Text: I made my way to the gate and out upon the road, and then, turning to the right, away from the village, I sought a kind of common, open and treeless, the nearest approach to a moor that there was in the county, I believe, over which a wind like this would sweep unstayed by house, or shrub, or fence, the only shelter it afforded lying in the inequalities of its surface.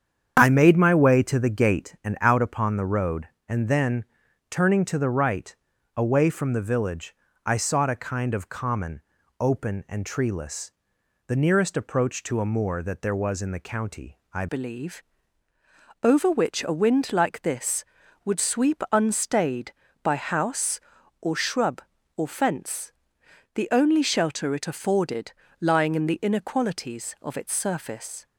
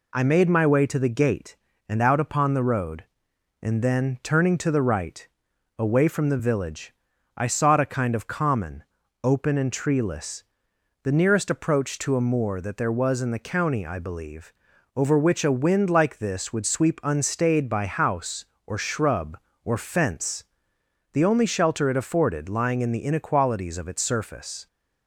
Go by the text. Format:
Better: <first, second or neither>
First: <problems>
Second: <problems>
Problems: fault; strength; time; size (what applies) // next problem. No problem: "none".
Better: second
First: starts louder than the rest; strong; until 1.3 s; 8 dB // changes voice at "believe"; from 14.4 s on; 13.8 s long // pauses between "afforded" and "lying"; slight; at 25.3 s; 0.26 s long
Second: none